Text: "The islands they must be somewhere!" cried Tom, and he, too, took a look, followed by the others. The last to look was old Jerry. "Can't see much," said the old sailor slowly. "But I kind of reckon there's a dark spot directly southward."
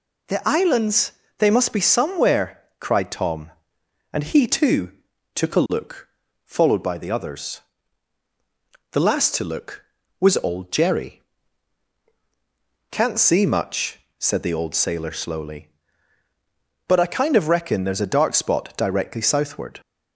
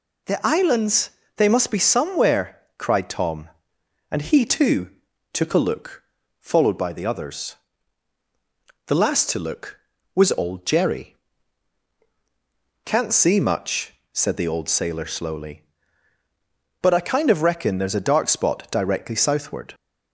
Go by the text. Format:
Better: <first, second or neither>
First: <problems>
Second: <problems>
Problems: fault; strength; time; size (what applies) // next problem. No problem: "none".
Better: neither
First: pauses between "islands" and "they"; slight; at 1.1 s; 0.26 s long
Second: pauses between "islands" and "they"; slight; at 1.1 s; 0.26 s long